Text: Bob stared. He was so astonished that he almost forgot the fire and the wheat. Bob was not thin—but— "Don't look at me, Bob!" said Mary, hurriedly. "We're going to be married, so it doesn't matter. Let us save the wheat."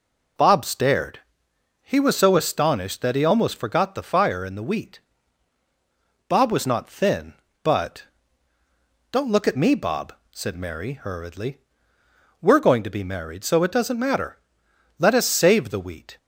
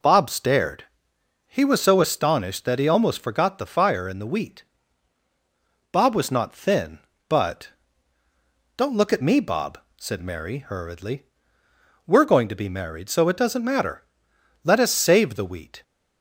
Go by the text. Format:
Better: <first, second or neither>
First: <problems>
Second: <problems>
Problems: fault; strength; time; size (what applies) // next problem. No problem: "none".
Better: neither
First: none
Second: none